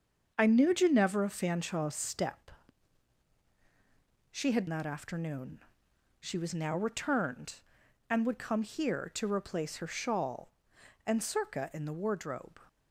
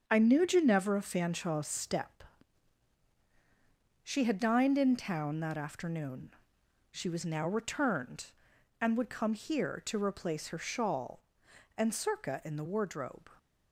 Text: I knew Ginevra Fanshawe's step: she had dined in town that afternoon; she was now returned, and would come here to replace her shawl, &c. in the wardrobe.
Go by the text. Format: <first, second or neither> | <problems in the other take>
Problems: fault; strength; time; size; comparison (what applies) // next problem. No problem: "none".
second | starts louder than the rest; until 1.3 s; 6.5 dB; also in the second // skips "dined in town"; at 4.6 s